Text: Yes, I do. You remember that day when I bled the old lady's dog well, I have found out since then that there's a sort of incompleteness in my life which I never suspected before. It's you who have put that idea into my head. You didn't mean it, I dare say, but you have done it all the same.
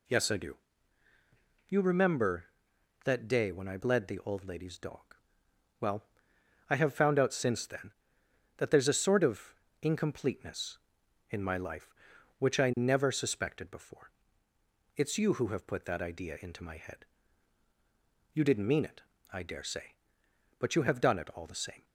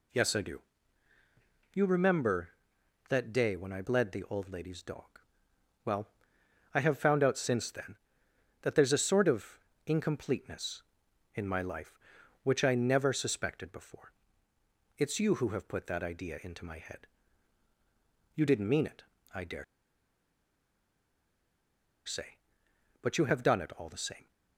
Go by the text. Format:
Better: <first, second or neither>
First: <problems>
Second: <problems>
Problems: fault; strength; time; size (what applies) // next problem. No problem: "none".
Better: first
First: pauses between "dog" and "well"; noticeable; at 4.9 s; 0.82 s long // pauses between "of" and "incompleteness"; slight; at 9.5 s; 0.30 s long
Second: pauses between "dog" and "well"; noticeable; at 5.0 s; 0.82 s long // pauses between "of" and "incompleteness"; slight; at 9.5 s; 0.30 s long // pauses between "dare" and "say"; strong; at 19.6 s; 2.4 s long